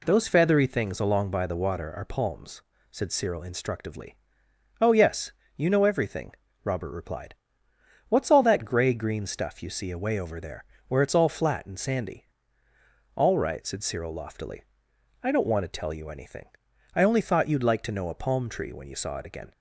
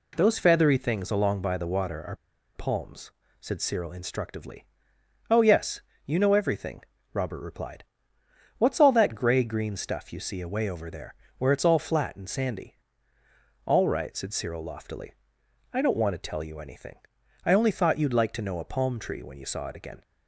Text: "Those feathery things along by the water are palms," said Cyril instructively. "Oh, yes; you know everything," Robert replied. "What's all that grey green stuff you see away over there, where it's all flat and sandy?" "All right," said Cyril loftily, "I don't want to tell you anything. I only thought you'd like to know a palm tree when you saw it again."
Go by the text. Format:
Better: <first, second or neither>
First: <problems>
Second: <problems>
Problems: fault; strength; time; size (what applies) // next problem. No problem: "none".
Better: first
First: none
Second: pauses between "are" and "palms"; at 2.1 s; 0.40 s long